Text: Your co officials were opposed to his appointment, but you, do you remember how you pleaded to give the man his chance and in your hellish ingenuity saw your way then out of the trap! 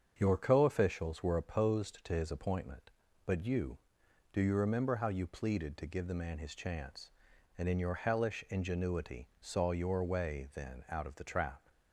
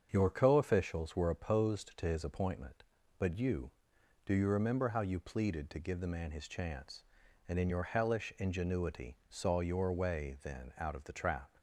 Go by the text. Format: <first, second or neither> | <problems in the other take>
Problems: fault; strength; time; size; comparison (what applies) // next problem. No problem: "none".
neither | starts louder than the rest; strong; the same in both